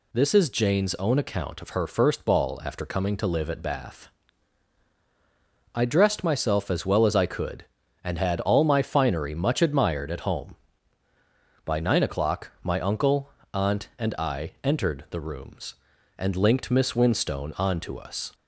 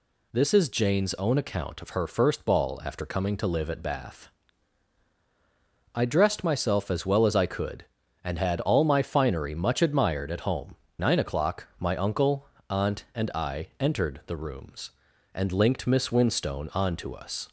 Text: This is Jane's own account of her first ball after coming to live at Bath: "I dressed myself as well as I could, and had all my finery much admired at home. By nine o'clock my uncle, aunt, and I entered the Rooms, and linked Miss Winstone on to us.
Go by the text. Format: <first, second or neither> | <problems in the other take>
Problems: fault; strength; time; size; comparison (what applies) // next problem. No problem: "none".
first | skips "By"; at 10.8 s